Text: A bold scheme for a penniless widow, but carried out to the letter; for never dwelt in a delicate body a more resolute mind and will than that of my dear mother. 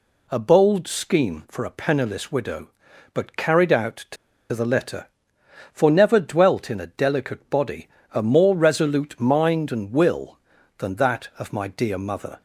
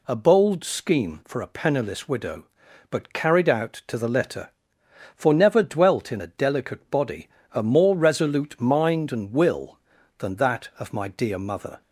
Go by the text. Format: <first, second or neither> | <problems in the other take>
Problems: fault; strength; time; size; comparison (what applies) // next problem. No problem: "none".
second | pauses between "to" and "the"; at 4.1 s; 0.36 s long // pauses between "body" and "a"; slight; at 7.8 s; 0.24 s long; slight in the second